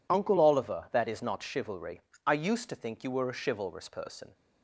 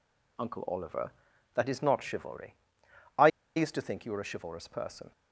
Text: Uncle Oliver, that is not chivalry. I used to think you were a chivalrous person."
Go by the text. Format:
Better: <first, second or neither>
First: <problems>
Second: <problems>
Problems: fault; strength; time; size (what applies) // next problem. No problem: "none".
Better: first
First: none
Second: pauses between "I" and "used"; slight; at 3.2 s; 0.28 s long